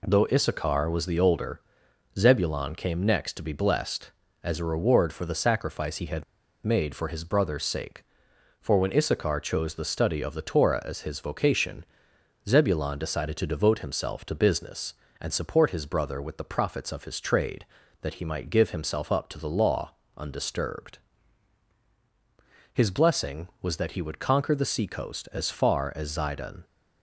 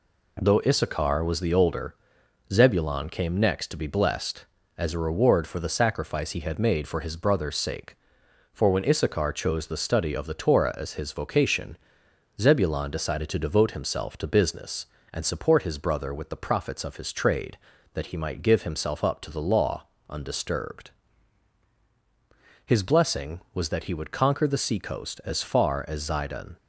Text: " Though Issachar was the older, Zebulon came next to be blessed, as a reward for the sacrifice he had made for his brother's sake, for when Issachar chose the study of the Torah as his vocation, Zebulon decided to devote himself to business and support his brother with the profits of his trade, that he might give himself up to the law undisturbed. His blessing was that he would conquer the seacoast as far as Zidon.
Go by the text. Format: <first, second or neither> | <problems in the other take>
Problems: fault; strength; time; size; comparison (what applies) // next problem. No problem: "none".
second | pauses between "had" and "made"; at 6.2 s; 0.41 s long // pauses between "law" and "undisturbed"; slight; at 19.9 s; 0.24 s long; slight in the second